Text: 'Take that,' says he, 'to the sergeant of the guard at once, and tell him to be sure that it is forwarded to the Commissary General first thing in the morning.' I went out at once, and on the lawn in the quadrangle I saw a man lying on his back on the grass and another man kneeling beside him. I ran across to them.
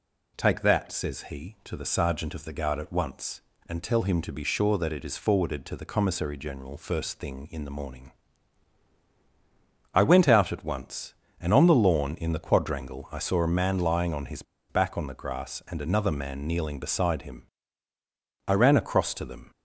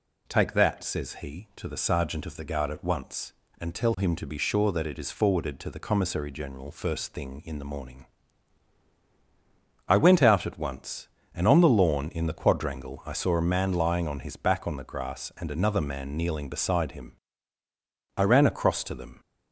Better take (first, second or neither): second